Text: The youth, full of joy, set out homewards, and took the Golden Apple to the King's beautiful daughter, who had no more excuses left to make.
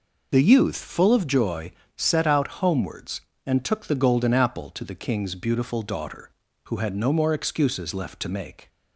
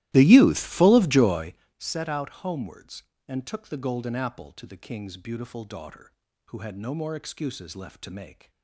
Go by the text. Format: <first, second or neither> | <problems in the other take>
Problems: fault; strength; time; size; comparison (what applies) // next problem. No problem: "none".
first | starts louder than the rest; strong; until 1.6 s; 16 dB